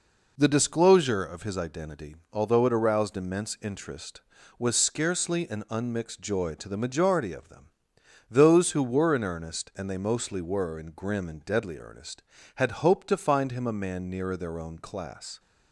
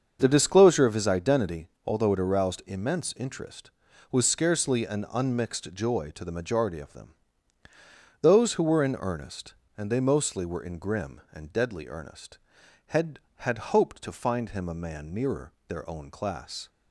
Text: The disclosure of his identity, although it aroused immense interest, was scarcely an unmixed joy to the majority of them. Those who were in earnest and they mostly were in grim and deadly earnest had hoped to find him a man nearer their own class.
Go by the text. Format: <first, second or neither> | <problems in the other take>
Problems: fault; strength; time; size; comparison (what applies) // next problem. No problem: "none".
first | starts louder than the rest; until 1.2 s; 6.5 dB // says "had" twice; at 13.3 s // pauses between "nearer" and "their"; slight; at 15.5 s; 0.16 s long